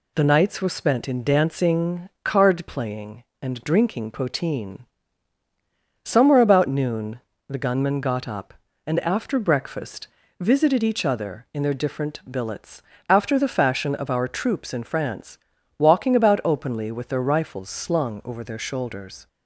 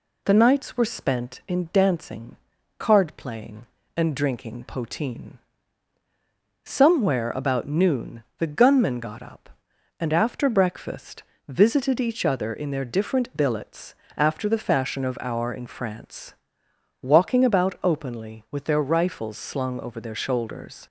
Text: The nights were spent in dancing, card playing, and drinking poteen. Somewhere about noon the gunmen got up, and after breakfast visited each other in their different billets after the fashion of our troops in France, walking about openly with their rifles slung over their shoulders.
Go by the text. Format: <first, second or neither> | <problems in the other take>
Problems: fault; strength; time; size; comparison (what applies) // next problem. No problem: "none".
first | pauses between "noon" and "the"; slight; at 8.2 s; 0.16 s long; slight in the first // pauses between "breakfast" and "visited"; slight; at 11.2 s; 0.24 s long; slight in the first // pauses between "billets" and "after"; slight; at 13.9 s; 0.20 s long; slight in the first // skips "troops"; at 15.5 s